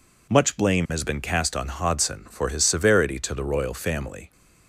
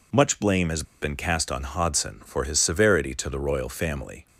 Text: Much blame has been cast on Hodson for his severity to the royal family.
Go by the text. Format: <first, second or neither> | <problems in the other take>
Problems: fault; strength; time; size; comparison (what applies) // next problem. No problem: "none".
first | pauses between "has" and "been"; slight; at 0.8 s; 0.19 s long